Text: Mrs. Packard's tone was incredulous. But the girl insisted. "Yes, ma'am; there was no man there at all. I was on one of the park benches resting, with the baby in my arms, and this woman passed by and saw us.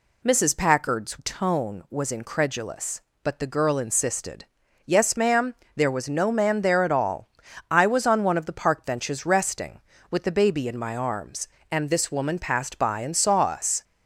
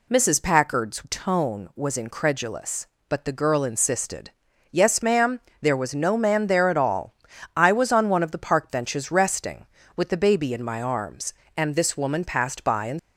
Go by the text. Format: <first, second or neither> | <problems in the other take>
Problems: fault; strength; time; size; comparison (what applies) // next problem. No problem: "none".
first | stops before "saw us"; at 12.9 s